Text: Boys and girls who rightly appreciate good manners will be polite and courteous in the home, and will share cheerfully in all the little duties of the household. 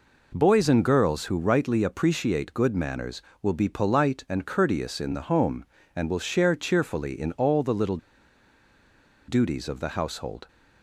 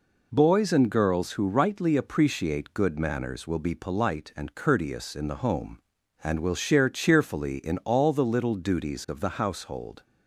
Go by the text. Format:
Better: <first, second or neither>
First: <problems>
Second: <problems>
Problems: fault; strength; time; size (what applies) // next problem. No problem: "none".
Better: second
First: pauses between "little" and "duties"; strong; at 7.9 s; 1.3 s long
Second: none